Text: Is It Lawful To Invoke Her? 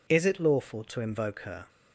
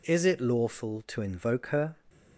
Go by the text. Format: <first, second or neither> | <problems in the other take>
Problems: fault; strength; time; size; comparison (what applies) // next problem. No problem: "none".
neither | none